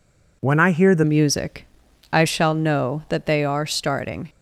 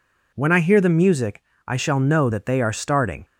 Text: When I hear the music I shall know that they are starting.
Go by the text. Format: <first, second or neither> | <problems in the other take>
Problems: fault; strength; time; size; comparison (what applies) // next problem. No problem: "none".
second | changes voice at "music"; from 1.0 s on; 3.2 s long // pauses between "music" and "I"; noticeable; at 1.6 s; 0.48 s long; slight in the second